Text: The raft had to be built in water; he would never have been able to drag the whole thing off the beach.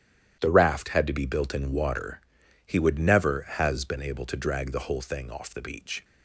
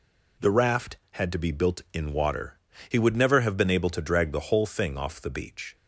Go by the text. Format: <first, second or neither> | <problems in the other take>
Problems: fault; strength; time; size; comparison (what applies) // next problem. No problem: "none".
second | starts louder than the rest; strong; until 1.4 s; 10.5 dB // says "has" for "have"; at 3.4 s